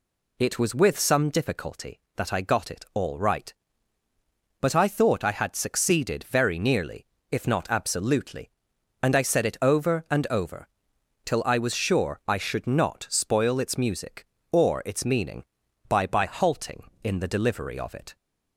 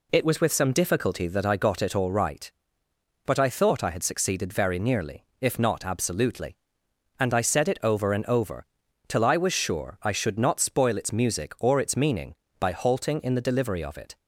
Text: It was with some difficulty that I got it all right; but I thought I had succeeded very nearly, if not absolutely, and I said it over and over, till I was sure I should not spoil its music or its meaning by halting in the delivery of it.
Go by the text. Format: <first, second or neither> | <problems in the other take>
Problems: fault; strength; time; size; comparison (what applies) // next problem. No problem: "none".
second | says "by" twice; at 16.0 s